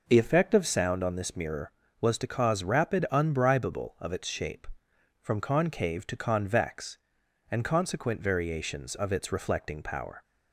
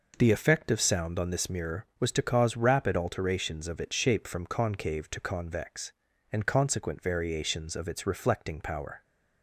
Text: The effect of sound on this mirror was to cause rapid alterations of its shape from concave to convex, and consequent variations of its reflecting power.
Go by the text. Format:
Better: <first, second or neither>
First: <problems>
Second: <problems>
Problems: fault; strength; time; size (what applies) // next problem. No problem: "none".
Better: second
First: says "unbribable" for "alterations"; at 3.1 s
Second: none